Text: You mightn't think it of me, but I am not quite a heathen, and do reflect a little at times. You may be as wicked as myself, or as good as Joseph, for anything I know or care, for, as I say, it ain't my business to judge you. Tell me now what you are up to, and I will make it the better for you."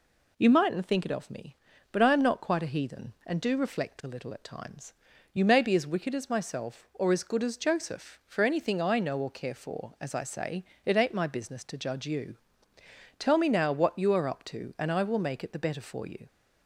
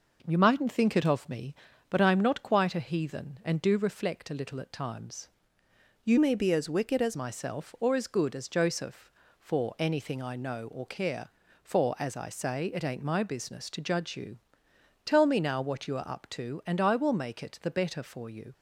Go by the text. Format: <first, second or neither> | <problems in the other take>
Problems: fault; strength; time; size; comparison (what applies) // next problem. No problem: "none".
first | changes voice from "may" to "as"; from 6.1 to 7.1 s; 1.0 s long